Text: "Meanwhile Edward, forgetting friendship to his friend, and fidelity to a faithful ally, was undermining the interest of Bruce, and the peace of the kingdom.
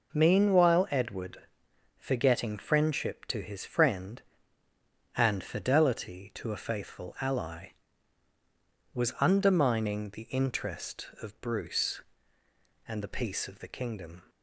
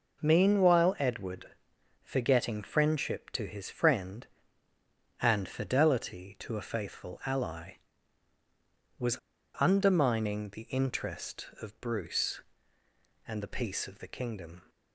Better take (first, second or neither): first